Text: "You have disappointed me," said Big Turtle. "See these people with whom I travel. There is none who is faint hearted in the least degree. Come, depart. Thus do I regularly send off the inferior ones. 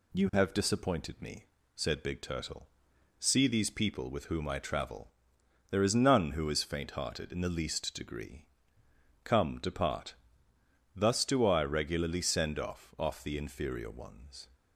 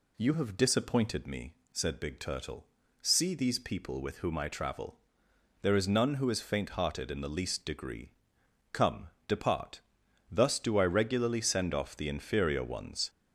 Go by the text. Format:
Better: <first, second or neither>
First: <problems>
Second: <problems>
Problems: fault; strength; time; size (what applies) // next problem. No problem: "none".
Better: second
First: says "off" twice; at 12.9 s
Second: none